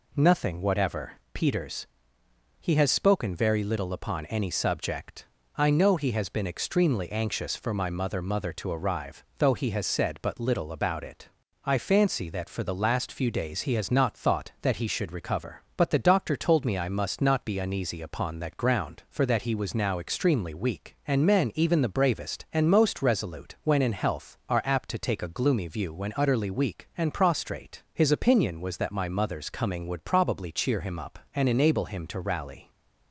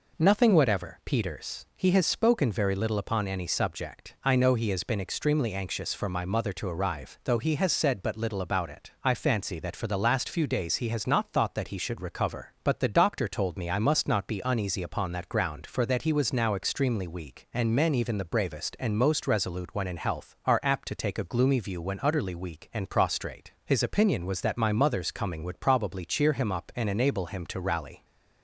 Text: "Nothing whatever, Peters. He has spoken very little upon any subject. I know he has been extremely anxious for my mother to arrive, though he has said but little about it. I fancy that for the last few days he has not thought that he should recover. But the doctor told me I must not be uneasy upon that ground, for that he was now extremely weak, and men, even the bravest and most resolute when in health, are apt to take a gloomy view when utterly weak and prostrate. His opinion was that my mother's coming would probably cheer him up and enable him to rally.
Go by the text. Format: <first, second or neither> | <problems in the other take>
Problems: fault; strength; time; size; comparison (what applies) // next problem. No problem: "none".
second | says "mother" twice; at 8.2 s